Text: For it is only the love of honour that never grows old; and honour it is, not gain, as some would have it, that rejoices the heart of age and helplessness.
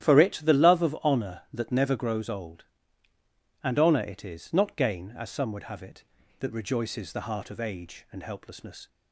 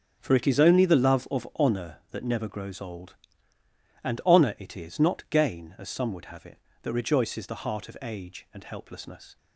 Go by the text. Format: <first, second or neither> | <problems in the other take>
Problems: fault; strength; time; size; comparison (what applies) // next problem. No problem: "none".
second | starts louder than the rest; strong; until 1.1 s; 11.5 dB; strong in the second // skips "is only"; at 0.4 s